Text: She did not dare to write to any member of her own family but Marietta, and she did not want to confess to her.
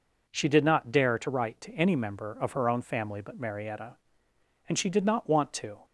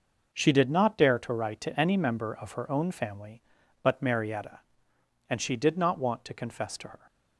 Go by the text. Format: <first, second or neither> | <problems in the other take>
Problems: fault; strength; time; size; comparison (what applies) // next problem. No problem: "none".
second | stops before "confess to her"; at 5.8 s